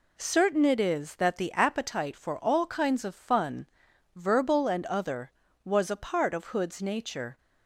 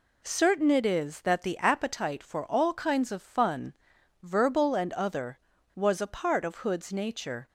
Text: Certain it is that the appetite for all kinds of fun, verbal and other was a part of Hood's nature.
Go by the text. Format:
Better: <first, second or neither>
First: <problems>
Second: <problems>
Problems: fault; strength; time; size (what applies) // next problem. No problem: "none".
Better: neither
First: none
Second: none